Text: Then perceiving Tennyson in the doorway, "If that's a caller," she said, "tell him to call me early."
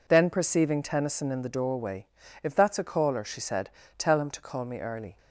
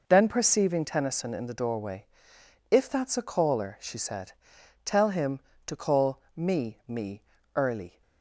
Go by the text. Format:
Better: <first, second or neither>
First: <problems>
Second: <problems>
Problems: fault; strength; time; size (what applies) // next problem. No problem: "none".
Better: first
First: none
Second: says "me" twice; at 6.8 s